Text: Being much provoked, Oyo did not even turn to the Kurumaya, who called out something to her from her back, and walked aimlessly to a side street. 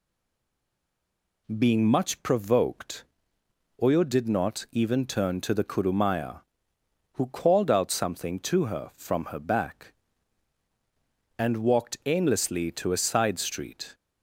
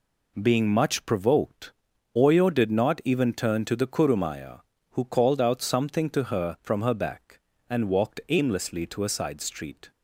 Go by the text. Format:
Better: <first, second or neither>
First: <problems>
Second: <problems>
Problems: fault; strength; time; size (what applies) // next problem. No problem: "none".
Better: second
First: stays silent before the first word; noticeable; until 1.4 s; 1.4 s long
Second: none